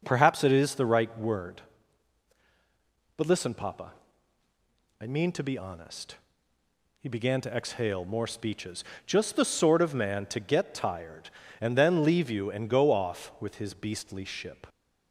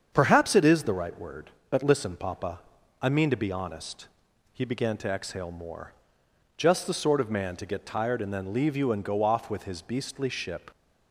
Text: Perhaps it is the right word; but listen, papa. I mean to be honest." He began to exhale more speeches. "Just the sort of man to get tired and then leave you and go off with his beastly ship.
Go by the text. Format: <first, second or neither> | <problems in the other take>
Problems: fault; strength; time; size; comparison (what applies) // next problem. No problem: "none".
first | starts louder than the rest; strong; until 1.1 s; 7.5 dB // skips "speeches"; at 6.2 s